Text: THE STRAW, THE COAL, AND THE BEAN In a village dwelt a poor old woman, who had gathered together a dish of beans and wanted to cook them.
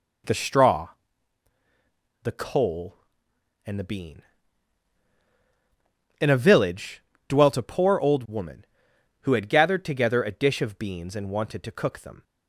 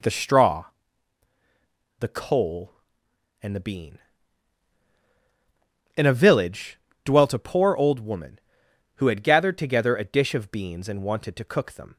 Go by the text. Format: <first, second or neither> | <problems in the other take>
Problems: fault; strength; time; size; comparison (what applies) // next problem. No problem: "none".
neither | pauses between "village" and "dwelt"; slight; the same in both